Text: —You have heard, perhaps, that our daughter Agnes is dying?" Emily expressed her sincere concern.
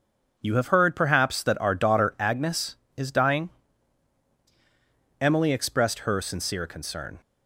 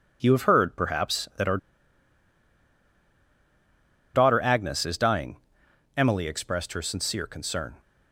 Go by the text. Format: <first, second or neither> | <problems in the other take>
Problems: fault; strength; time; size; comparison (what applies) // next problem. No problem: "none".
first | pauses between "our" and "daughter"; strong; at 1.5 s; 2.5 s long